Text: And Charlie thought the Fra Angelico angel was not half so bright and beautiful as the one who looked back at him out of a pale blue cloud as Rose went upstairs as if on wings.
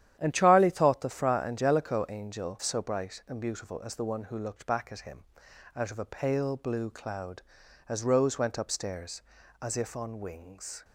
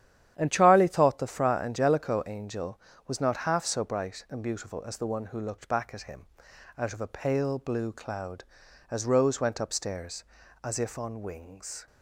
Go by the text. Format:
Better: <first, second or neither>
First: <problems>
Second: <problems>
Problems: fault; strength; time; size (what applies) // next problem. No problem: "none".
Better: second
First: starts louder than the rest; strong; until 1.2 s; 10.5 dB // skips "was not half"; at 2.6 s // pauses between "him" and "out"; noticeable; at 5.2 s; 0.52 s long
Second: starts louder than the rest; strong; until 1.3 s; 10.5 dB // pauses between "him" and "out"; noticeable; at 6.2 s; 0.52 s long